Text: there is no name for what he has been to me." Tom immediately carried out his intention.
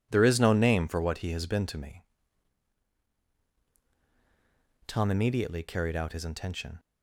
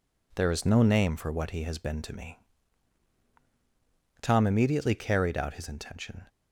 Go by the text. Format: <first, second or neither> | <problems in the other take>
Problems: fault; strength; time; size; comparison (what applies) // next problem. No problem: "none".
neither | none